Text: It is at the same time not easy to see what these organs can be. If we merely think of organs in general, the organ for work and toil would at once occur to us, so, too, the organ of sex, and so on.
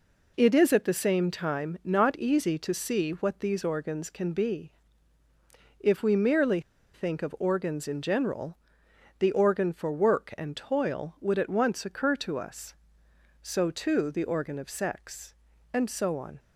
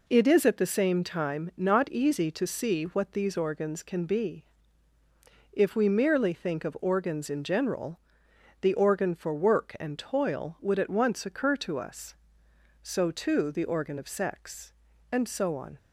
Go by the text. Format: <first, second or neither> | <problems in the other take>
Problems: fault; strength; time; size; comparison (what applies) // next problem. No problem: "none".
second | pauses between "merely" and "think"; slight; at 6.5 s; 0.33 s long